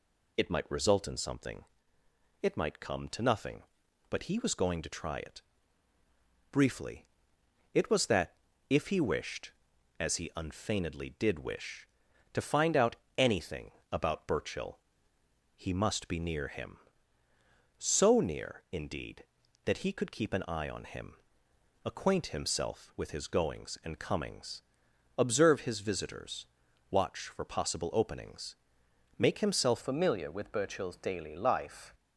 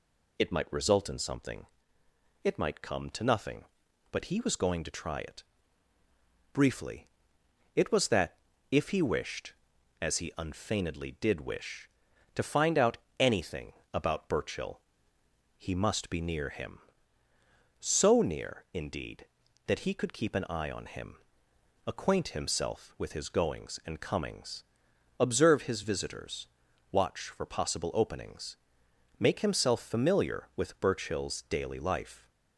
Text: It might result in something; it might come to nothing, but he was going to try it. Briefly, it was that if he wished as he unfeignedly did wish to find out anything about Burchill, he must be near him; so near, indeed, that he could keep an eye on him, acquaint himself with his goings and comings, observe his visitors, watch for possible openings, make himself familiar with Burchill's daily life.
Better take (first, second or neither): second